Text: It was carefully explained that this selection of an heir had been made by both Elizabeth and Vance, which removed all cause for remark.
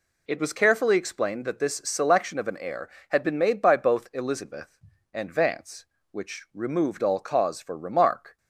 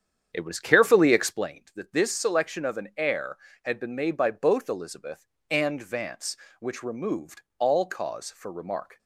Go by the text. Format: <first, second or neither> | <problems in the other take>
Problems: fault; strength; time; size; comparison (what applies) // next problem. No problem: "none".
first | starts louder than the rest; strong; until 1.5 s; 8.5 dB // pauses between "removed" and "all"; slight; at 7.4 s; 0.16 s long